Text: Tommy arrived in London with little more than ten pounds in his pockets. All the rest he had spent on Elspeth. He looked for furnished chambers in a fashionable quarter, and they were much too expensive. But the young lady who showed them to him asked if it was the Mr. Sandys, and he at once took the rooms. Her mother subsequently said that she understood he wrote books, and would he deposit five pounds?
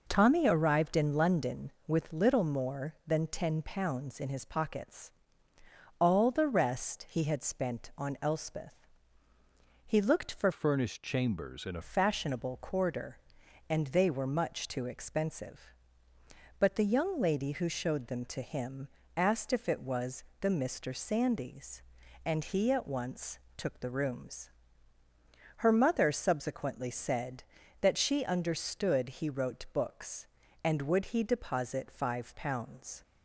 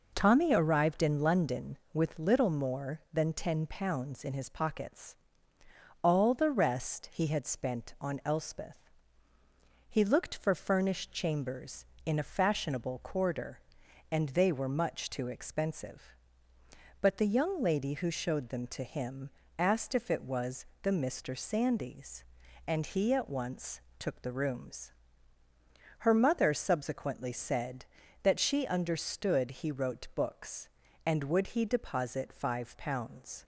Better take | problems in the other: second | changes voice from "furnished" to "a"; from 10.5 to 11.8 s; 1.3 s long // pauses between "him" and "asked"; slight; at 18.8 s; 0.26 s long; slight in the second // pauses between "was" and "the"; slight; at 20.2 s; 0.18 s long; slight in the second // pauses between "once" and "took"; slight; at 23.3 s; 0.16 s long; slight in the second

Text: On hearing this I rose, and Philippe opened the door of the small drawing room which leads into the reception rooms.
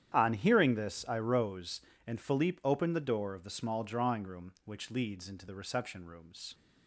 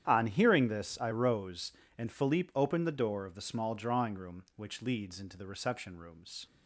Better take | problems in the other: neither | starts louder than the rest; strong; the same in both

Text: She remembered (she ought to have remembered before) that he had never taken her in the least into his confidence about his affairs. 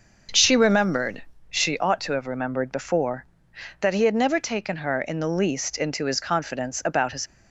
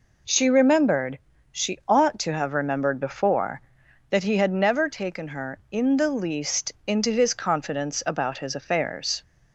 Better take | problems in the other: second | starts louder than the rest; noticeable; until 1.5 s; 6 dB // stops before "affairs"; at 7.2 s

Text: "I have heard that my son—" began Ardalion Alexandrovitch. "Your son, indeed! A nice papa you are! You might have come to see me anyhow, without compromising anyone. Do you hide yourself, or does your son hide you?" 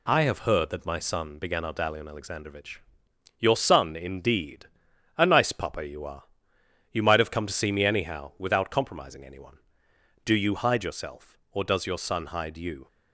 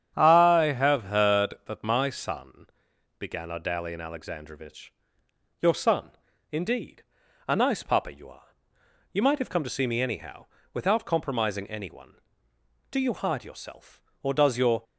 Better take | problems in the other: first | starts louder than the rest; strong; until 1.1 s; 9 dB // stops before "son hide you"; at 14.8 s

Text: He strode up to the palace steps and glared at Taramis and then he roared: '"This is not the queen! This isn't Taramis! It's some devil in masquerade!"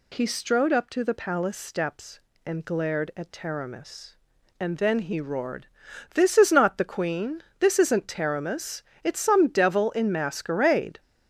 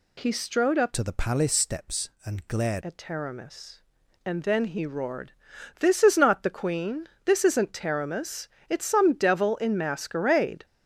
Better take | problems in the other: first | changes voice from "to" to "glared"; from 0.9 to 2.8 s; 1.9 s long

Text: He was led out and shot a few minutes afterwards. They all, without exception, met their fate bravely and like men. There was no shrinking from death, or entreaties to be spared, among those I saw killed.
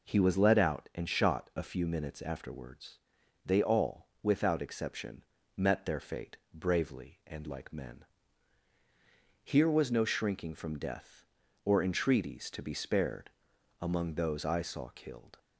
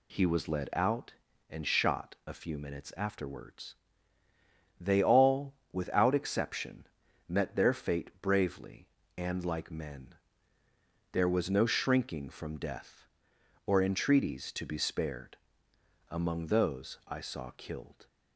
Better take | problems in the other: second | pauses between "fate" and "bravely"; slight; at 6.3 s; 0.18 s long // says "Here" for "There"; at 9.4 s

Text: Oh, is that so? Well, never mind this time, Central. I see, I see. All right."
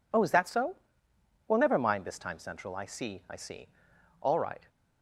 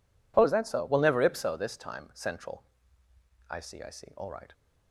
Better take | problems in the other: first | says "ipso" for "mind"; at 1.2 s

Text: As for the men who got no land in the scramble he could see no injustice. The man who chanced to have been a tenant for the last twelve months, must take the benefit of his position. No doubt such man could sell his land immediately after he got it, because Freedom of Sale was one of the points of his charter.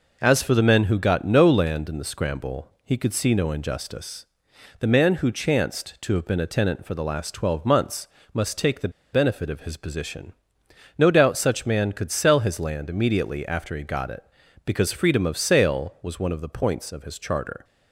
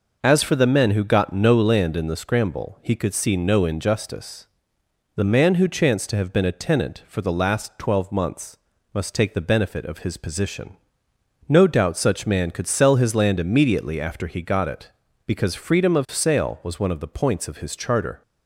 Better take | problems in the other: second | pauses between "the" and "benefit"; slight; at 8.8 s; 0.24 s long

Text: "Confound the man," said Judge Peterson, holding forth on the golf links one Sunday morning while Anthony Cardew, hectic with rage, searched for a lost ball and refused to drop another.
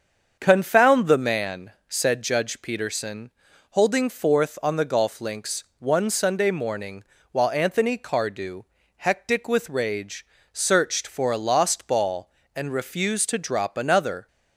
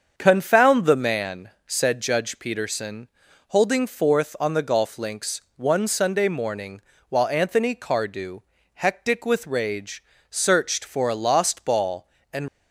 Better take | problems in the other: first | starts louder than the rest; until 1.1 s; 7 dB; also in the first // pauses between "links" and "one"; slight; at 5.4 s; 0.16 s long; slight in the first // pauses between "morning" and "while"; slight; at 6.8 s; 0.28 s long; slight in the first // stops before "refused to drop another"; at 12.4 s

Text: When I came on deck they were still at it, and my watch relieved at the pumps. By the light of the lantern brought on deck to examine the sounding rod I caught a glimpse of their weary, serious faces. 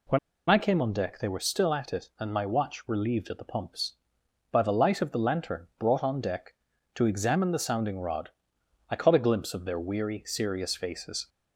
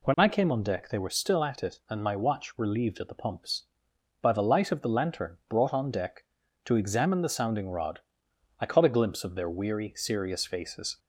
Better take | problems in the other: second | pauses between "When" and "I"; slight; at 0.1 s; 0.31 s long // pauses between "rod" and "I"; noticeable; at 8.2 s; 0.62 s long; noticeable in the second

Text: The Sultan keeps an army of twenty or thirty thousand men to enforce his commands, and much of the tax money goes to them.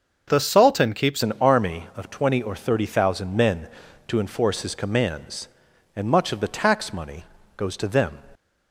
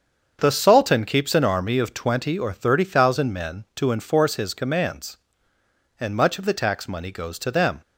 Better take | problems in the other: second | starts louder than the rest; until 1.2 s; 6.5 dB; also in the second // changes voice at "an"; from 1.2 s on; 7.0 s long // pauses between "money" and "goes"; slight; at 7.2 s; 0.32 s long

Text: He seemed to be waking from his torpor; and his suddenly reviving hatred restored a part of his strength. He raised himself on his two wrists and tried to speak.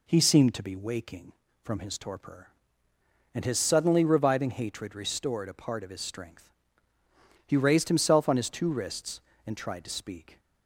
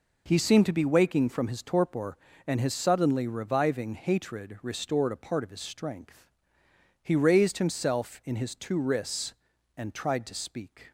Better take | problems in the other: first | says "in" for "on"; at 8.2 s

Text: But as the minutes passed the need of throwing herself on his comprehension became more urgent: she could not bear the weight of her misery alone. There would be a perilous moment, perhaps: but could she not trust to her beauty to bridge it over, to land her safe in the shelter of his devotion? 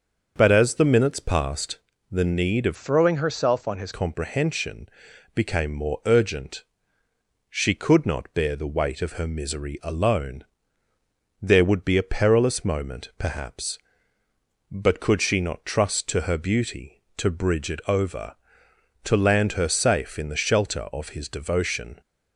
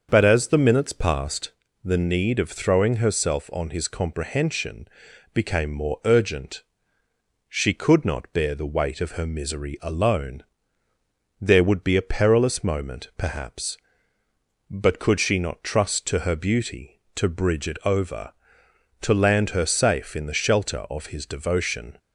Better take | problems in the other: second | starts louder than the rest; until 1.3 s; 6 dB; also in the second // pauses between "passed" and "the"; slight; at 1.7 s; 0.30 s long; slight in the second // changes voice from "throwing" to "his"; from 2.7 to 3.9 s; 1.2 s long // pauses between "comprehension" and "became"; noticeable; at 4.8 s; 0.48 s long; noticeable in the second

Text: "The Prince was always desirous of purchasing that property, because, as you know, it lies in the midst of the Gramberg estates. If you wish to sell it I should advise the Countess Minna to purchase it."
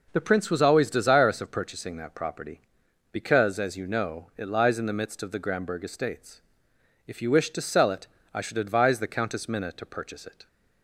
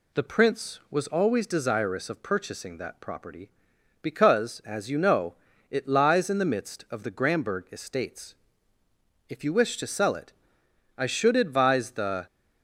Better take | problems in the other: first | pauses between "it" and "I"; noticeable; at 10.3 s; 0.64 s long; slight in the first // stops before "Countess Minna to purchase it"; at 12.2 s

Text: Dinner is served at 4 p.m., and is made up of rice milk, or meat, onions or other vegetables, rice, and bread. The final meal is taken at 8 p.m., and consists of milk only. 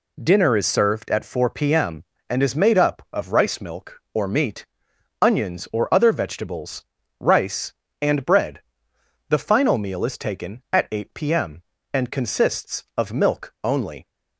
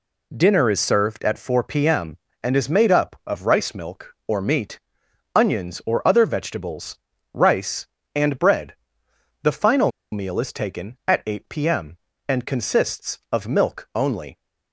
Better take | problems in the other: first | pauses between "final" and "meal"; slight; at 9.9 s; 0.21 s long

